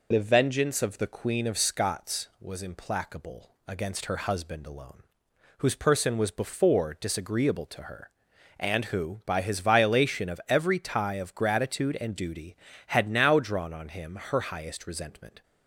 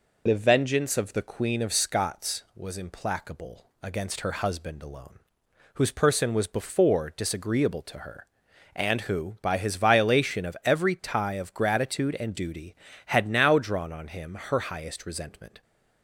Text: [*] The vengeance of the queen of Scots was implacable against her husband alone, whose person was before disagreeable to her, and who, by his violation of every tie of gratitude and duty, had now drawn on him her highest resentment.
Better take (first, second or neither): neither